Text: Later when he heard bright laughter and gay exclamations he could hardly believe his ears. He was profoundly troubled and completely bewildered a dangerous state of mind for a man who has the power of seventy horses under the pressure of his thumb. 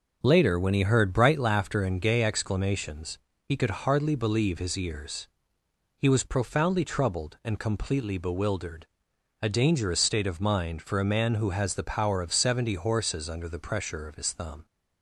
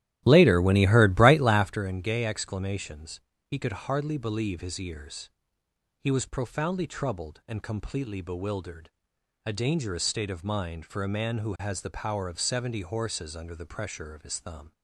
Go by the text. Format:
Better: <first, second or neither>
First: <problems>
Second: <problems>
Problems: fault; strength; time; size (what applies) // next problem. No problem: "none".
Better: first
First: pauses between "exclamations" and "he"; slight; at 3.1 s; 0.32 s long // pauses between "bewildered" and "a"; noticeable; at 8.8 s; 0.56 s long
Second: starts louder than the rest; strong; until 1.8 s; 13.5 dB // pauses between "exclamations" and "he"; slight; at 3.1 s; 0.32 s long // pauses between "bewildered" and "a"; noticeable; at 8.8 s; 0.56 s long